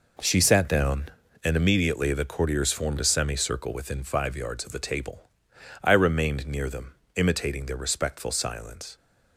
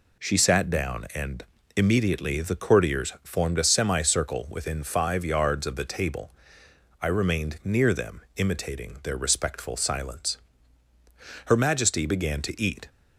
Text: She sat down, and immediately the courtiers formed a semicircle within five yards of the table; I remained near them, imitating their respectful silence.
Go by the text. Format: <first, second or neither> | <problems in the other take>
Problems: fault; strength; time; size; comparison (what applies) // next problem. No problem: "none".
first | pauses between "and" and "immediately"; slight; at 1.4 s; 0.32 s long // goes on to say "Her majesty began to eat"; from 11.4 s on; 1.4 s long